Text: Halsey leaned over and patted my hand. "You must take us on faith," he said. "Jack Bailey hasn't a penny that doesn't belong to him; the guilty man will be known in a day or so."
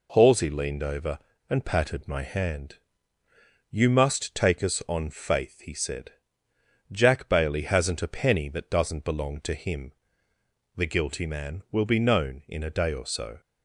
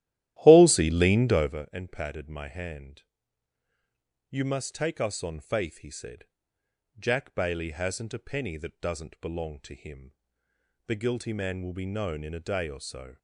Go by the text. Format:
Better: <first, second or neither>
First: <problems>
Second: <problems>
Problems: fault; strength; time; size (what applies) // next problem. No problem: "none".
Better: first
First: none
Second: starts louder than the rest; strong; until 1.6 s; 13.5 dB